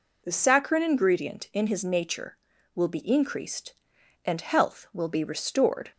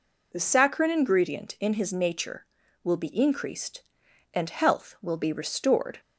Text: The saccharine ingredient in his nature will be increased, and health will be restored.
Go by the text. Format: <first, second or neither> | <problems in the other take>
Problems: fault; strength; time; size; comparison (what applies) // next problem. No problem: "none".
neither | none